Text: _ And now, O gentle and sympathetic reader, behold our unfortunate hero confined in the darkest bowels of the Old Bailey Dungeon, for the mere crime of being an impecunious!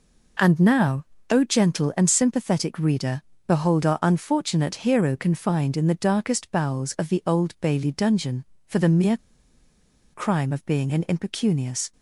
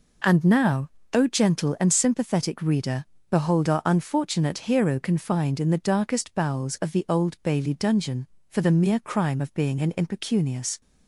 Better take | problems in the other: second | pauses between "mere" and "crime"; noticeable; at 9.1 s; 0.96 s long

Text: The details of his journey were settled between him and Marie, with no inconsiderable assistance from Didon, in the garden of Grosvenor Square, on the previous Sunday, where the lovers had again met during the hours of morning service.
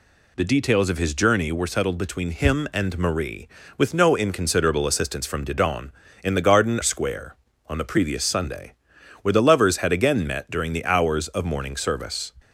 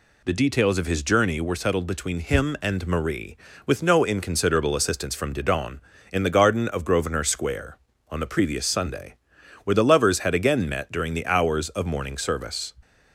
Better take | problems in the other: second | skips "of Grosvenor"; at 6.8 s

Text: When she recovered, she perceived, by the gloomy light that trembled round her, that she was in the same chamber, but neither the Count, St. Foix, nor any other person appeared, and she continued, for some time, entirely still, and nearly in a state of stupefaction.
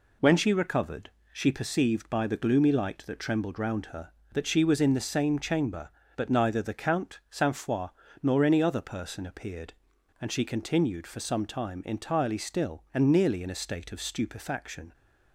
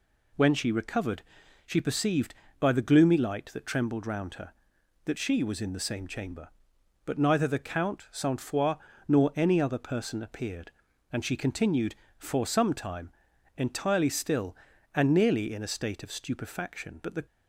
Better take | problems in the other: first | goes on to say "But the"; slight; from 17.0 s on; 0.24 s long

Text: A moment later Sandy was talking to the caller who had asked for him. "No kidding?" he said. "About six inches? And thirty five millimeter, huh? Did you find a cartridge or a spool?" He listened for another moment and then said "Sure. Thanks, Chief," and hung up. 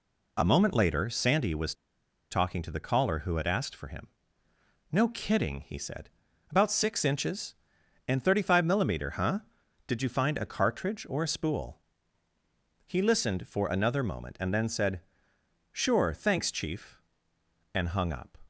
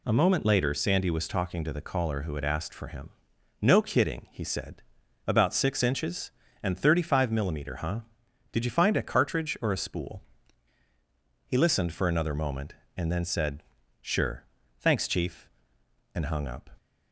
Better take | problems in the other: second | pauses between "was" and "talking"; noticeable; at 1.7 s; 0.56 s long // pauses between "said" and "Sure"; noticeable; at 14.9 s; 0.72 s long; also in the second

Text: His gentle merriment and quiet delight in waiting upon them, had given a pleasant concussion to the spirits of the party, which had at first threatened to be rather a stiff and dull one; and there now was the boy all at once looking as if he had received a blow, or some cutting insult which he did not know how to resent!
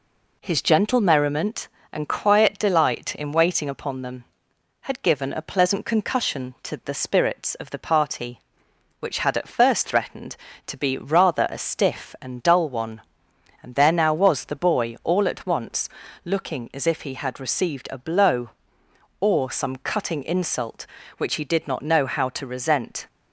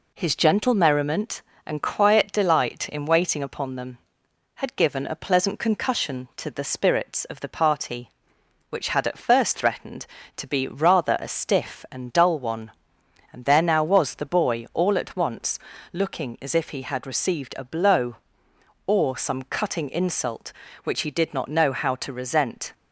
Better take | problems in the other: neither | pauses between "once" and "looking"; slight; the same in both

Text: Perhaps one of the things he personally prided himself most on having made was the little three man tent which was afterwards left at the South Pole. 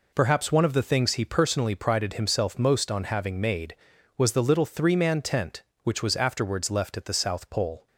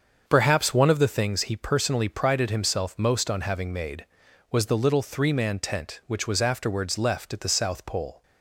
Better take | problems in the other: first | starts louder than the rest; until 1.3 s; 7 dB

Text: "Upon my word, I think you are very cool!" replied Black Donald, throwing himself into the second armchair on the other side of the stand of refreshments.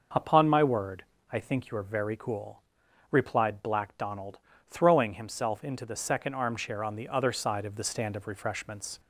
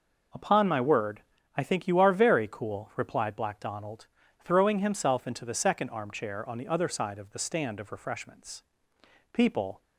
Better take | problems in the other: first | goes on to say "People"; slight; from 9.3 s on; 0.48 s long

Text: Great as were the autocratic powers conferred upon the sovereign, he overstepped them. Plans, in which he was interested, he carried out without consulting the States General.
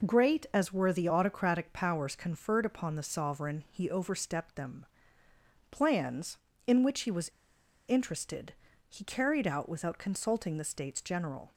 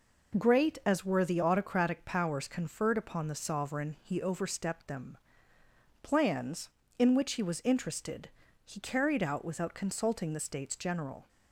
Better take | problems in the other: second | pauses between "was" and "interested"; noticeable; at 7.2 s; 0.58 s long

